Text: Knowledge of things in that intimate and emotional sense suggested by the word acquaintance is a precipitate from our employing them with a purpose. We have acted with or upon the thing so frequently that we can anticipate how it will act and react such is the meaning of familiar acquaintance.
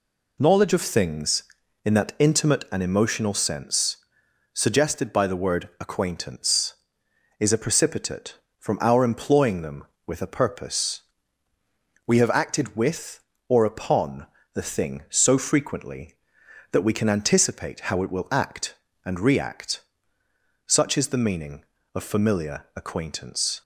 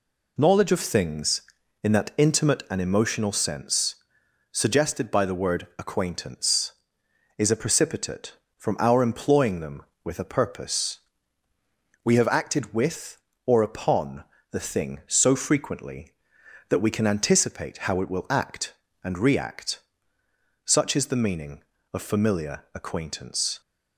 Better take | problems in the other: neither | pauses between "sense" and "suggested"; noticeable; the same in both // pauses between "upon" and "the"; slight; the same in both // pauses between "react" and "such"; noticeable; the same in both

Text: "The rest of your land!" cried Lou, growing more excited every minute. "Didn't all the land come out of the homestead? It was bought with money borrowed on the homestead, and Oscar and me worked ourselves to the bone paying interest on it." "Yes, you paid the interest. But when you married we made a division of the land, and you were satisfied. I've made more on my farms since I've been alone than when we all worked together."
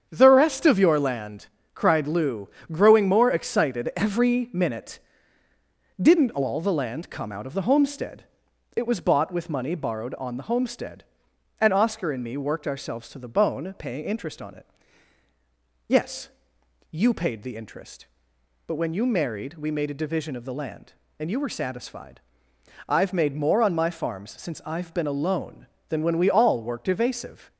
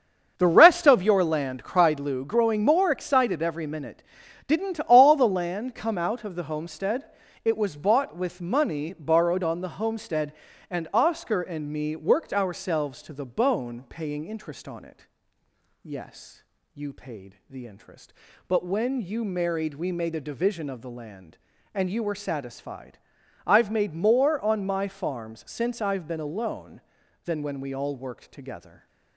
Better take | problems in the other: second | starts louder than the rest; strong; until 1.1 s; 8 dB; also in the second // says "evasive" for "together"; at 26.8 s

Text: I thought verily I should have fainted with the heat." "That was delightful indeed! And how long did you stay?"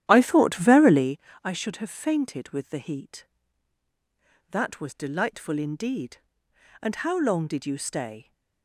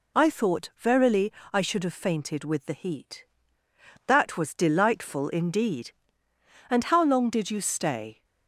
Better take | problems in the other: second | starts louder than the rest; strong; until 1.2 s; 11.5 dB // pauses between "verily" and "I"; slight; at 1.1 s; 0.24 s long; slight in the second

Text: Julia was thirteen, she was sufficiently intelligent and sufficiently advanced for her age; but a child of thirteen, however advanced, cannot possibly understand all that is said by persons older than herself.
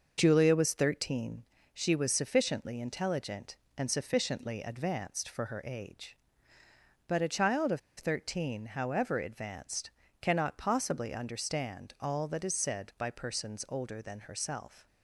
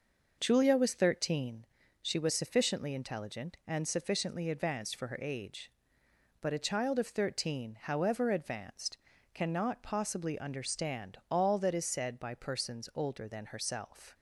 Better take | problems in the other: second | starts louder than the rest; noticeable; until 1.1 s; 6 dB // pauses between "of" and "thirteen"; slight; at 7.7 s; 0.18 s long

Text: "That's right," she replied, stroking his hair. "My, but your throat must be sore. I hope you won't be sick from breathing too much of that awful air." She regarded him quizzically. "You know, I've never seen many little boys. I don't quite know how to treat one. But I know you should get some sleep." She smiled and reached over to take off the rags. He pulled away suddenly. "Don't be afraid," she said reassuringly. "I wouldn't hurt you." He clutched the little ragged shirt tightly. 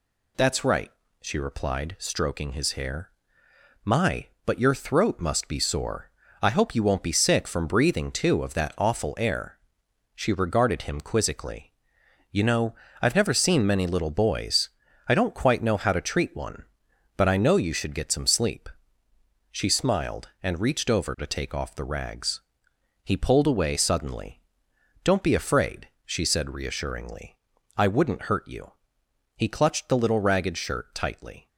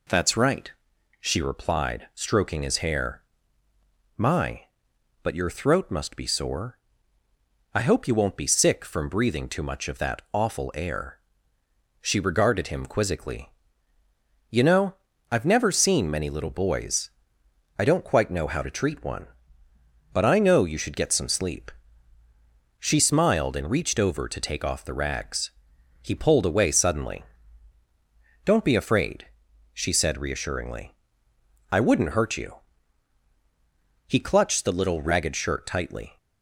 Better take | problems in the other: second | skips "much"; at 8.4 s

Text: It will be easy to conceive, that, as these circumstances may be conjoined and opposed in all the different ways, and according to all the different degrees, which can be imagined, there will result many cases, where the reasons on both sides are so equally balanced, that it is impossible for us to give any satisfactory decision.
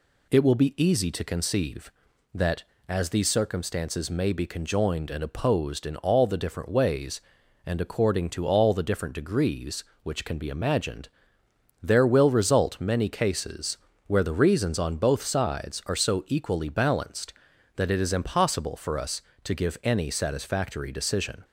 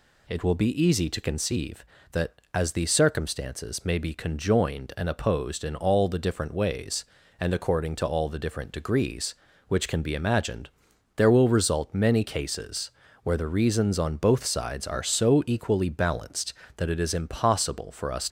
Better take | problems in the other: first | stops before "to give any satisfactory decision"; at 18.2 s

